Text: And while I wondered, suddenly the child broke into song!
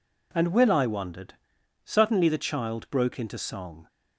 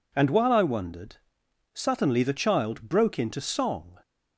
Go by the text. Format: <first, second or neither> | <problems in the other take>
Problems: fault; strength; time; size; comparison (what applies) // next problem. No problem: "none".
second | says "will" for "while"; at 0.4 s